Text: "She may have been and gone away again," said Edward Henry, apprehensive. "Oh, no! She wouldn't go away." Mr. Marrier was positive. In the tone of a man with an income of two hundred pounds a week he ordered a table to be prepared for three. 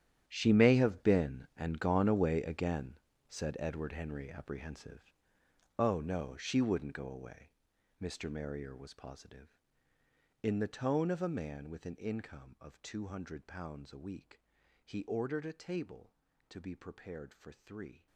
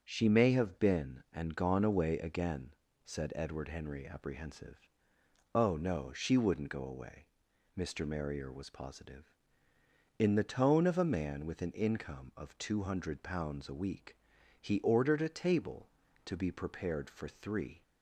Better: second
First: gets quieter; strong; throughout; 15.5 dB // starts louder than the rest; strong; until 1.2 s; 10.5 dB // pauses between "week" and "he"; at 14.4 s; 0.44 s long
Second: starts louder than the rest; until 1.0 s; 6.5 dB // pauses between "week" and "he"; at 14.1 s; 0.44 s long

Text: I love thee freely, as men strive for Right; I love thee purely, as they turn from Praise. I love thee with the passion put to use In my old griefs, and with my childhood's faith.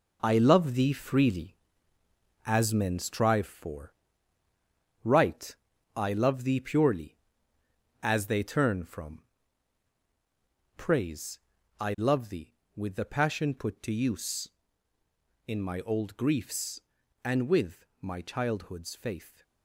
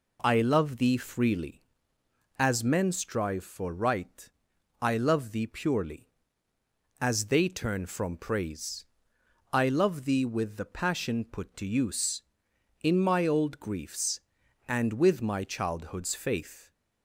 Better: second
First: gets quieter; strong; throughout; 8 dB // pauses between "for" and "Right"; at 3.9 s; 1.0 s long // pauses between "from" and "Praise"; strong; at 9.2 s; 1.5 s long // pauses between "with" and "my"; slight; at 17.8 s; 0.16 s long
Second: none

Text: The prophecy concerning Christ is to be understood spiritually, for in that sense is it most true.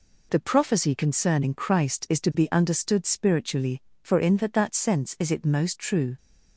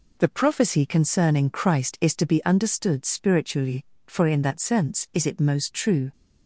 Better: second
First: says "that" twice; at 4.5 s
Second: none

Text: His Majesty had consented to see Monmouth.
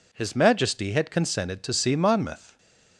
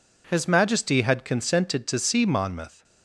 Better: neither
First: none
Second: none

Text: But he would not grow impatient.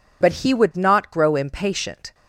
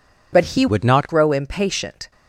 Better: first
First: none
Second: changes voice from "would" to "not"; from 0.6 to 1.0 s; 0.4 s long

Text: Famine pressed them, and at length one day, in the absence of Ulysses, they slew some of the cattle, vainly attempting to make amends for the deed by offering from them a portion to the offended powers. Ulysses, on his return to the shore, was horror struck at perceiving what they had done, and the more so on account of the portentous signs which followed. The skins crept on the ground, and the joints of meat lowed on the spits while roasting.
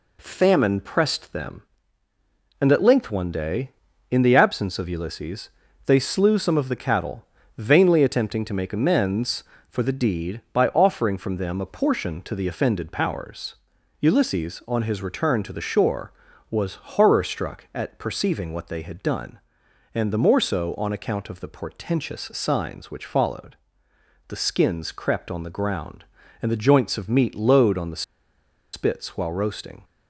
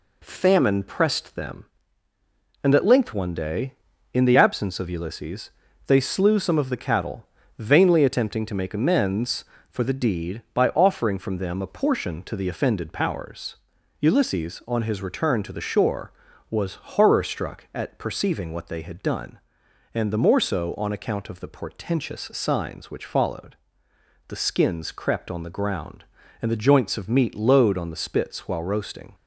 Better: second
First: pauses between "the" and "spits"; noticeable; at 28.0 s; 0.71 s long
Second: none

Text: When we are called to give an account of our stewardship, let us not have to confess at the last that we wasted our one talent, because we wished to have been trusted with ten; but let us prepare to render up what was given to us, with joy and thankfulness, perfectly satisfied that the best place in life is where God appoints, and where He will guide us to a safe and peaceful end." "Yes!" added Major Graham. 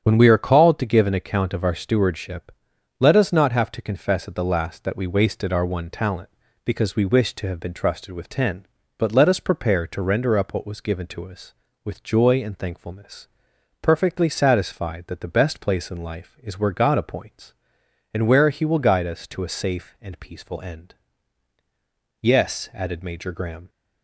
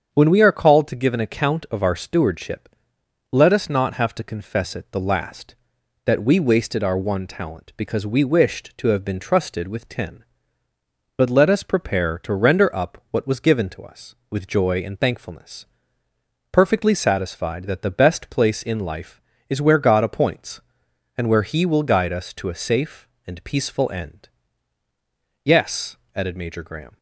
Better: first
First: starts louder than the rest; strong; until 1.0 s; 9 dB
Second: starts louder than the rest; strong; until 1.1 s; 7.5 dB // says "it" for "at"; at 4.7 s

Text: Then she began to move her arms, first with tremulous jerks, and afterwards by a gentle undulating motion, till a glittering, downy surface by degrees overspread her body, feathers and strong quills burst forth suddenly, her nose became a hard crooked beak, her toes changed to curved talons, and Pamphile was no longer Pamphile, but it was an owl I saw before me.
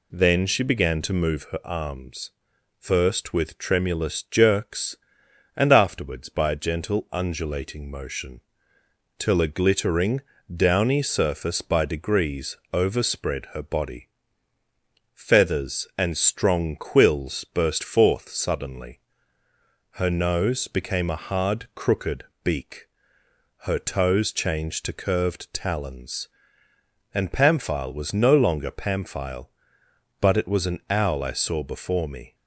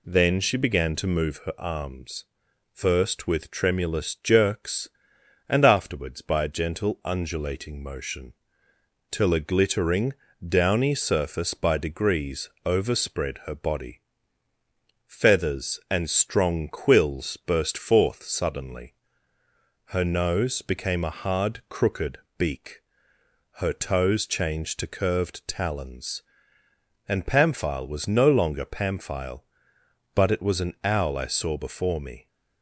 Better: neither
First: pauses between "degrees" and "overspread"; slight; at 12.5 s; 0.16 s long // pauses between "crooked" and "beak"; slight; at 22.2 s; 0.22 s long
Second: pauses between "degrees" and "overspread"; slight; at 12.4 s; 0.16 s long // pauses between "crooked" and "beak"; slight; at 22.1 s; 0.22 s long

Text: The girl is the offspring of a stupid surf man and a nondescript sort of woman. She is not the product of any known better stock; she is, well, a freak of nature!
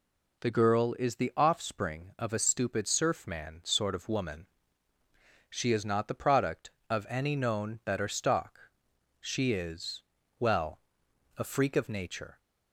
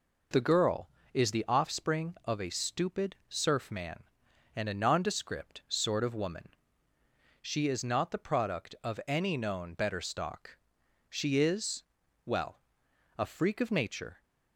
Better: second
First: skips "and a nondescript"; at 3.6 s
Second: none

